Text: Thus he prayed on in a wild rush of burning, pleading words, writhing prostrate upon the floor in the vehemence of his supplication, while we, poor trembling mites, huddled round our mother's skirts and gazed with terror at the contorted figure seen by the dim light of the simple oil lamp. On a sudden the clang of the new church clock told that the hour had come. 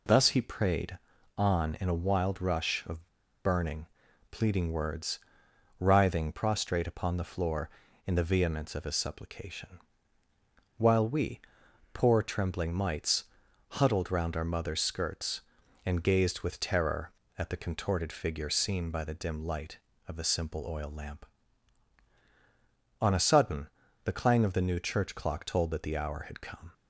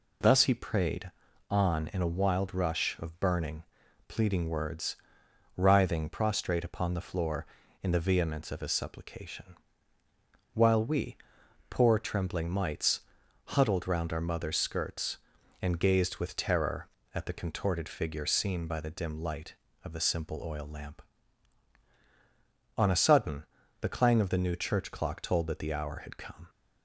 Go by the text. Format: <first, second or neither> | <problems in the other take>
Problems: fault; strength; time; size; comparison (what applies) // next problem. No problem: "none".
second | pauses between "of" and "burning"; at 3.0 s; 0.39 s long // pauses between "sudden" and "the"; at 23.6 s; 0.38 s long; also in the second